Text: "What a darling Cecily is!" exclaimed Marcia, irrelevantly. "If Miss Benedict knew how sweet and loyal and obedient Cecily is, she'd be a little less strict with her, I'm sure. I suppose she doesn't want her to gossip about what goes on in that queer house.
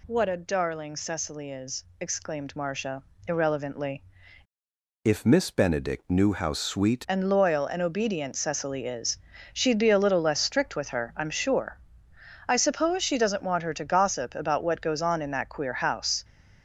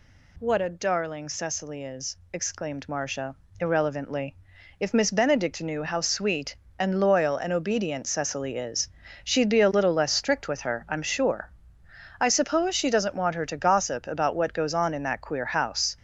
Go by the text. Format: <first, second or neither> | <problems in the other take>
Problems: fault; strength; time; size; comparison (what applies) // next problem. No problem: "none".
second | changes voice from "If" to "sweet"; from 5.0 to 7.0 s; 2.0 s long